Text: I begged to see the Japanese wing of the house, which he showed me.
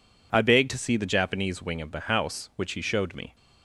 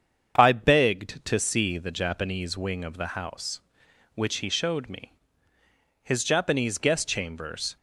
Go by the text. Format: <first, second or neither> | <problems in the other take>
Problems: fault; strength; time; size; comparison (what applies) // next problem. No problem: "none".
first | starts louder than the rest; strong; until 1.3 s; 7.5 dB // goes on to say "His Japanese guest chambers"; strong; from 6.0 s on; 1.7 s long